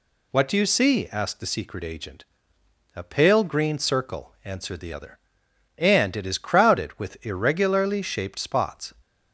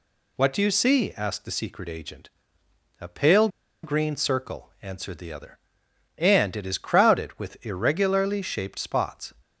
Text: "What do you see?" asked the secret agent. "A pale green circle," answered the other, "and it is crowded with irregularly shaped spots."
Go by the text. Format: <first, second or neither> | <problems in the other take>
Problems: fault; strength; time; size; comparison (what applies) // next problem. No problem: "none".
first | pauses between "pale" and "green"; slight; at 3.4 s; 0.34 s long